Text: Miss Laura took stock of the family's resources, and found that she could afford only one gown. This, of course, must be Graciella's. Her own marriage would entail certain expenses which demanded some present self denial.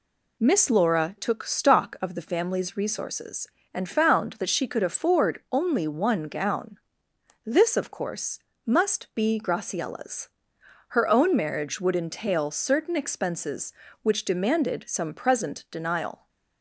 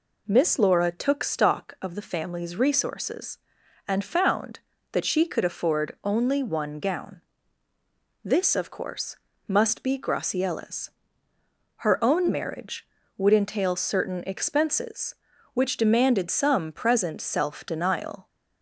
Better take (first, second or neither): second